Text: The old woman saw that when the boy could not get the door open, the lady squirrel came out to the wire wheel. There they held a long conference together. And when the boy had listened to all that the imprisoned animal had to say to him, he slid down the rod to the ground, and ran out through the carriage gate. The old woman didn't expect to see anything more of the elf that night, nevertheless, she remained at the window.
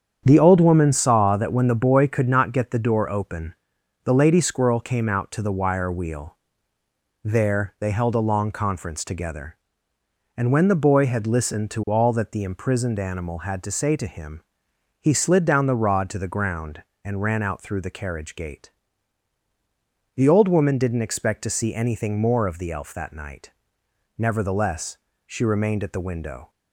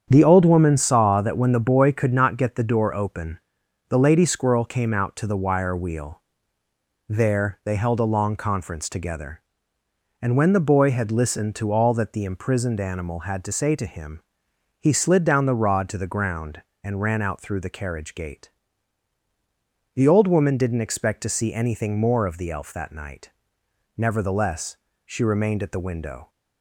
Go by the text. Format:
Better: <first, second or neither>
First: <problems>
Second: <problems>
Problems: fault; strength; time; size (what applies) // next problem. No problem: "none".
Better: neither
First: starts louder than the rest; strong; until 1.2 s; 8 dB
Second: starts louder than the rest; strong; until 1.1 s; 8 dB